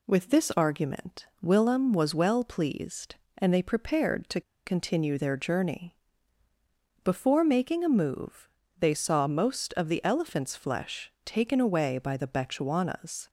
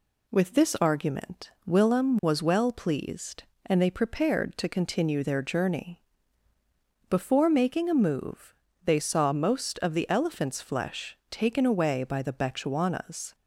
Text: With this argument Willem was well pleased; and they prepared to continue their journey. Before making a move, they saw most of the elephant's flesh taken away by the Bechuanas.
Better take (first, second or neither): second